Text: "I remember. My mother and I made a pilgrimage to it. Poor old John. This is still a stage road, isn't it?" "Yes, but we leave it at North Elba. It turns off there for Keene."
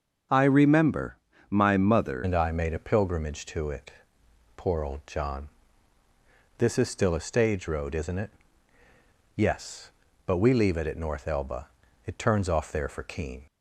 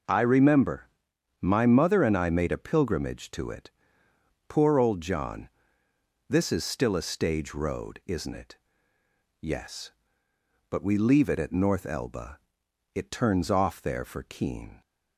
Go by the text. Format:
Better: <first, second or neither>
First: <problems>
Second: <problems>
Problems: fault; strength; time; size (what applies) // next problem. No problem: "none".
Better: second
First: starts louder than the rest; until 1.6 s; 6.5 dB // changes voice at "and"; from 2.2 s on; 11.2 s long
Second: none